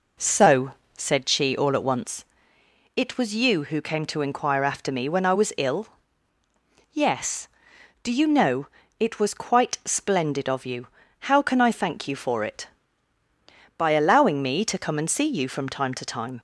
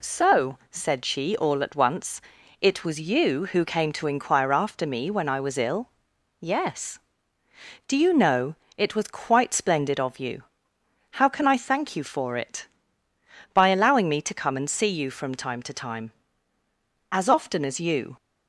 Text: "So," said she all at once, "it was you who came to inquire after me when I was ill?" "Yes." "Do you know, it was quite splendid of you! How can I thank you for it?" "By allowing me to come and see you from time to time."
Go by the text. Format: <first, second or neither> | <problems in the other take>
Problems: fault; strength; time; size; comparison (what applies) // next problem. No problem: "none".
first | goes on to say "As often as you"; noticeable; from 17.0 s on; 1.0 s long